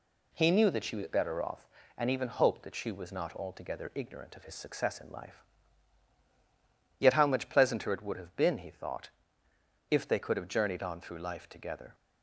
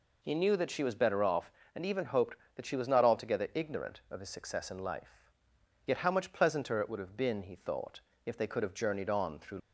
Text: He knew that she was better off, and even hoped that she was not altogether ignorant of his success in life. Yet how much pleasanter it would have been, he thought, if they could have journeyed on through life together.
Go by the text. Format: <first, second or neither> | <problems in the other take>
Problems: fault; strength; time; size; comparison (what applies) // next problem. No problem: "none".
first | stops before "life together"; at 9.5 s